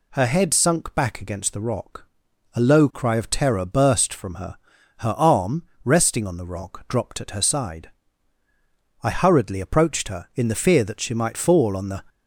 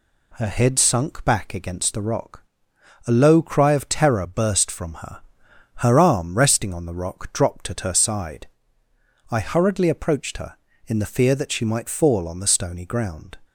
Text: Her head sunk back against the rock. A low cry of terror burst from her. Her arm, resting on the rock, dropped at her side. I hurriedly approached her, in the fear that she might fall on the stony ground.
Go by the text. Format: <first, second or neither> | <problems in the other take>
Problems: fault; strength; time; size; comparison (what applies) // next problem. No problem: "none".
second | stops before "stony ground"; at 12.0 s